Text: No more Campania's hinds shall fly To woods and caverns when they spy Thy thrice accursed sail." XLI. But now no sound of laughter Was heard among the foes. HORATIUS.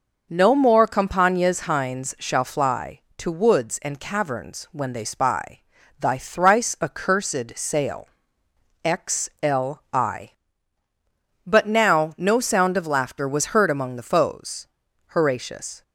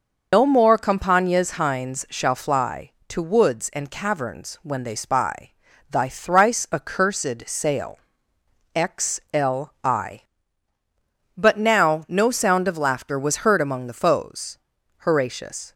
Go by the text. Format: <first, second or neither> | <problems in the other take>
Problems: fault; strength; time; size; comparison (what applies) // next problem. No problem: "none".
first | loses the start of "No"; at 0.3 s; 115 ms // pauses between "spy" and "Thy"; at 5.5 s; 0.40 s long; also in the first